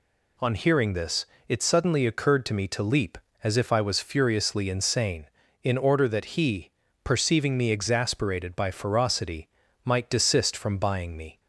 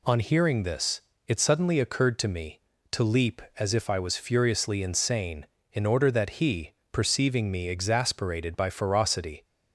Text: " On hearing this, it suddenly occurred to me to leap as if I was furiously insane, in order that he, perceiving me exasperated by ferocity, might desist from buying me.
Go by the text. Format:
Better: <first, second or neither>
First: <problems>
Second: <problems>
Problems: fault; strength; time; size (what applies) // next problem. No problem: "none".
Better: first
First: none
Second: stops before "might desist from buying me"; at 9.4 s